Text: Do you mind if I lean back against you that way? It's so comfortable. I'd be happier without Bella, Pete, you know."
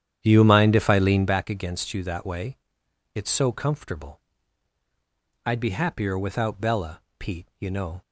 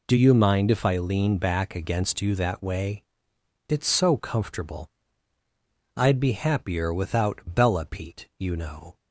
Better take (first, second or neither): second